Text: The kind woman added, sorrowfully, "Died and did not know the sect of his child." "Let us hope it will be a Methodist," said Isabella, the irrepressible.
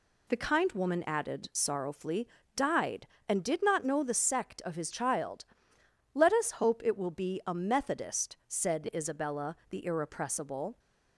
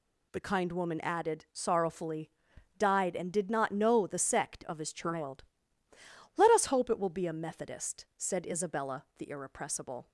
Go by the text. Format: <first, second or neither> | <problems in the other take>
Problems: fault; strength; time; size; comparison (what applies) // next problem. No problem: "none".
neither | none